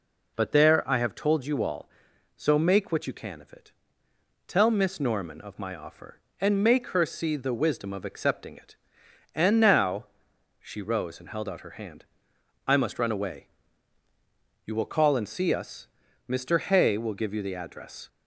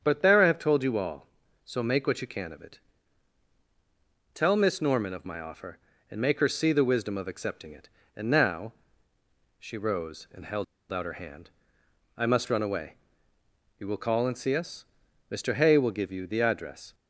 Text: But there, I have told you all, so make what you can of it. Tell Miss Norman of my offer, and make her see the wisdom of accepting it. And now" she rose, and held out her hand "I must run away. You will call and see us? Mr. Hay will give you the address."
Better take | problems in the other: first | starts louder than the rest; strong; until 1.0 s; 7.5 dB // pauses between "now" and "she"; noticeable; at 8.7 s; 0.86 s long; noticeable in the first // pauses between "held" and "out"; slight; at 10.6 s; 0.27 s long // pauses between "hand" and "I"; noticeable; at 11.4 s; 0.68 s long; noticeable in the first

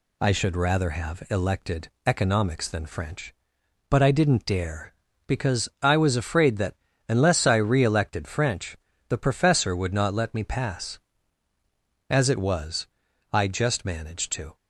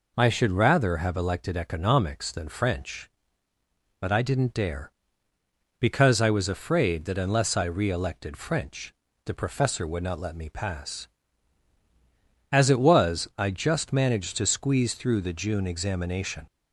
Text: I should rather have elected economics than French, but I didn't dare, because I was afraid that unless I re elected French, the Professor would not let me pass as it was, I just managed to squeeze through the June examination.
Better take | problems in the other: second | pauses between "elected" and "economics"; slight; at 1.8 s; 0.16 s long // pauses between "that" and "unless"; slight; at 6.7 s; 0.34 s long // stops before "squeeze through the June examination"; at 14.5 s

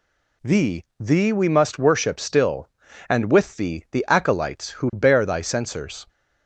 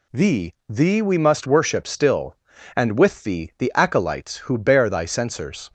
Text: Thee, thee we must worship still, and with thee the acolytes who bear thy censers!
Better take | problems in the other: neither | none

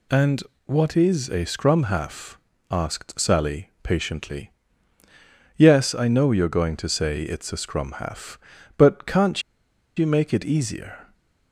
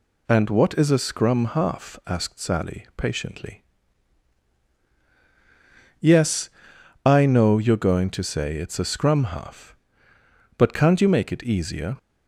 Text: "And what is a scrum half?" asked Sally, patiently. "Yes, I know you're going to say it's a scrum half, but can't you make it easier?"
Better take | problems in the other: second | pauses between "And" and "what"; slight; at 0.4 s; 0.24 s long // pauses between "can't" and "you"; noticeable; at 9.4 s; 0.55 s long

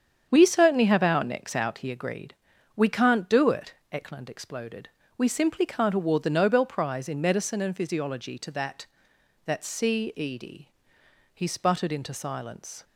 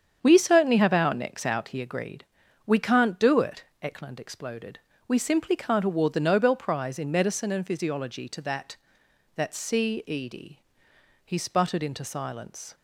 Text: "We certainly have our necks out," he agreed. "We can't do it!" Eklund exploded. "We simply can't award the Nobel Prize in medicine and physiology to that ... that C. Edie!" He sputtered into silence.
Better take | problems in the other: neither | starts louder than the rest; strong; the same in both

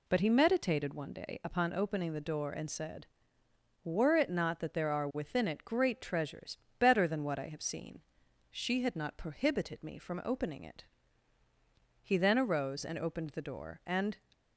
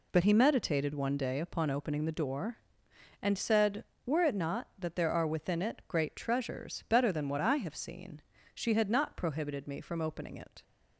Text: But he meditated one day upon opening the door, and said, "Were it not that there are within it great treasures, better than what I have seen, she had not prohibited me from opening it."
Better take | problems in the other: second | goes on to say "He then arose and opened the door and"; strong; from 12.0 s on; 2.1 s long

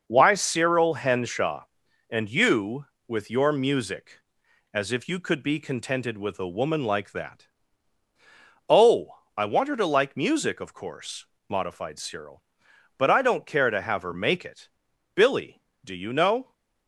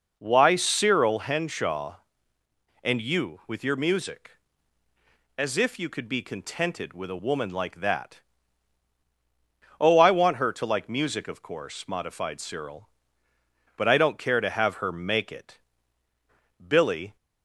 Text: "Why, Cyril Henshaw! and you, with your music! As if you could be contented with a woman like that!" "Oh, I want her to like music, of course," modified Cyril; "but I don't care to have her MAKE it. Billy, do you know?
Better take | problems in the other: first | stops before "do you know"; at 17.1 s

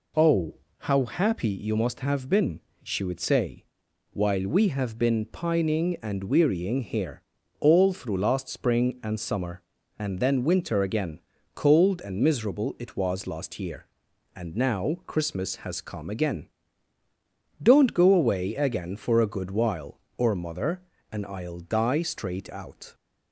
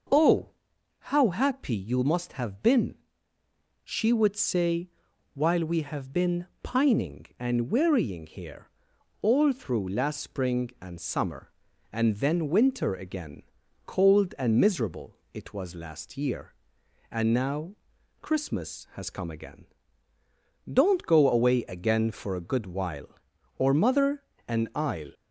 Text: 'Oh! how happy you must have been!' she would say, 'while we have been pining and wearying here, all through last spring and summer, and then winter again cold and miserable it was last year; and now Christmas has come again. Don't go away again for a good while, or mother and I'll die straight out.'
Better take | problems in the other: first | pauses between "been" and "pining"; slight; at 6.4 s; 0.16 s long // pauses between "again" and "cold"; at 13.4 s; 0.44 s long; slight in the first // pauses between "miserable" and "it"; slight; at 15.1 s; 0.16 s long // pauses between "now" and "Christmas"; noticeable; at 17.7 s; 0.46 s long // stops before "die straight out"; at 25.1 s

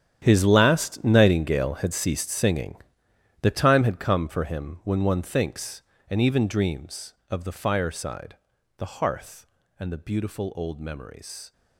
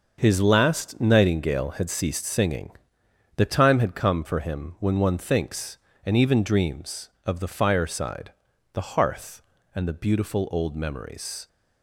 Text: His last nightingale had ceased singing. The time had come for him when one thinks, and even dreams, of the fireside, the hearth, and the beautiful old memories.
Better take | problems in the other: second | gets quieter; strong; throughout; 16 dB // starts louder than the rest; strong; until 1.2 s; 9.5 dB; noticeable in the second

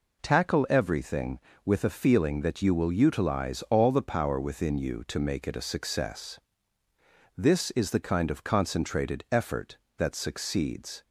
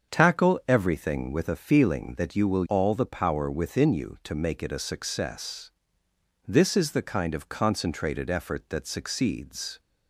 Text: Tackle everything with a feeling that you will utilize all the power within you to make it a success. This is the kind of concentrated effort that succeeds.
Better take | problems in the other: first | starts louder than the rest; until 1.1 s; 7 dB // skips "utilize"; at 2.6 s

